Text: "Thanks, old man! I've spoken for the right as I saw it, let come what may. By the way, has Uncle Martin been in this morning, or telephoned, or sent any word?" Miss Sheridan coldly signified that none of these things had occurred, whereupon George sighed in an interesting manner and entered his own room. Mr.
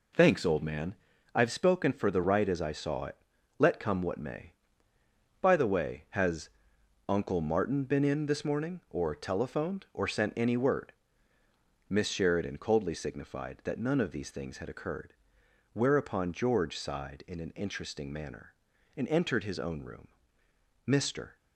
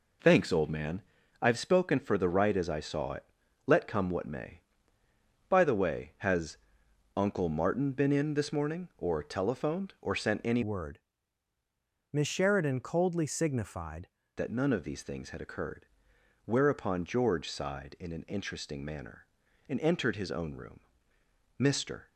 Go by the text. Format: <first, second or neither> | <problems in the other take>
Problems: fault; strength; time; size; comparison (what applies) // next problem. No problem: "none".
first | pauses between "has" and "Uncle"; noticeable; at 6.5 s; 0.58 s long; noticeable in the first // changes voice from "word" to "signified"; from 10.6 to 14.0 s; 3.4 s long